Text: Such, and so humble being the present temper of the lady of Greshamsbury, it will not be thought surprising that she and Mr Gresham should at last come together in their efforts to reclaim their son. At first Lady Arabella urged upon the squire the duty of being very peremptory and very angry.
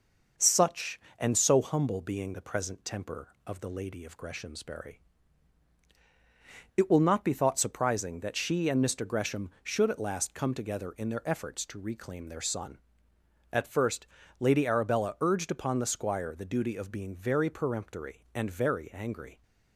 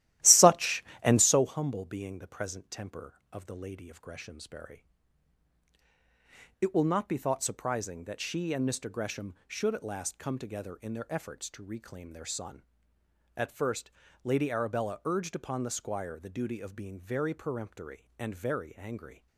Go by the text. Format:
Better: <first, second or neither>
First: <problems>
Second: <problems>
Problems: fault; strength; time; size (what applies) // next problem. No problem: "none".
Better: first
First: pauses between "first" and "Lady"; slight; at 14.0 s; 0.34 s long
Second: starts louder than the rest; strong; until 1.5 s; 14.5 dB // pauses between "first" and "Lady"; slight; at 13.9 s; 0.34 s long